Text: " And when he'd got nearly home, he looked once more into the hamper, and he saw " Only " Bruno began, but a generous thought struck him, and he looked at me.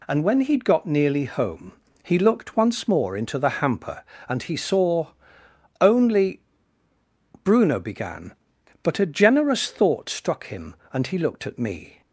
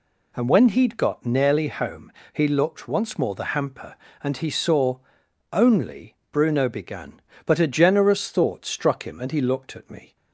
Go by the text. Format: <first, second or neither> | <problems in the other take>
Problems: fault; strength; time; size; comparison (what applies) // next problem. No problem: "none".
first | skips "into"; at 3.3 s